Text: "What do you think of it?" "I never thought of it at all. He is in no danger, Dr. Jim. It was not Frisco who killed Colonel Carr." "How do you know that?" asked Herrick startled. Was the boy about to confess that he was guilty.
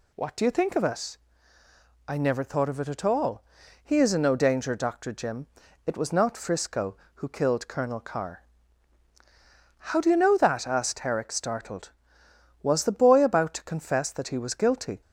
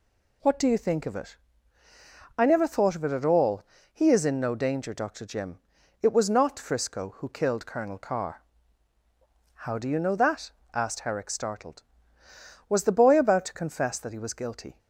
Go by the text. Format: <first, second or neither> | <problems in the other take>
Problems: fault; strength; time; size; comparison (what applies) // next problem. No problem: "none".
neither | none